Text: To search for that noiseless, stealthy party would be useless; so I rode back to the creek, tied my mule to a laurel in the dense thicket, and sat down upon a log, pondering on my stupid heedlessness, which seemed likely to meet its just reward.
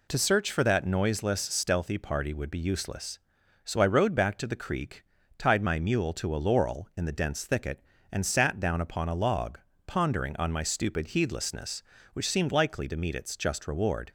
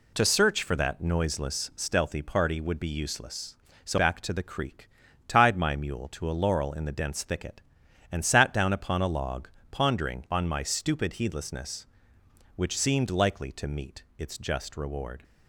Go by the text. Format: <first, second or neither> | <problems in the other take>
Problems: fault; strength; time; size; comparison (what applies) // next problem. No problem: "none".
first | skips "I rode"; at 3.9 s // pauses between "meet" and "its"; slight; at 14.0 s; 0.16 s long